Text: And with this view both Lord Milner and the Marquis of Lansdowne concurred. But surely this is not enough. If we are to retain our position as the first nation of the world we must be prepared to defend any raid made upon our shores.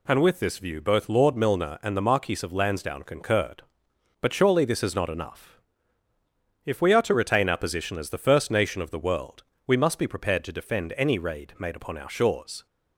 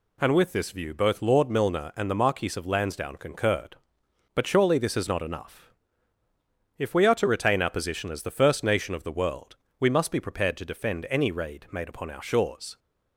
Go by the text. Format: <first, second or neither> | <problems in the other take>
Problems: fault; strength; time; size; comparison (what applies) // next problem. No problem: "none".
neither | pauses between "world" and "we"; slight; the same in both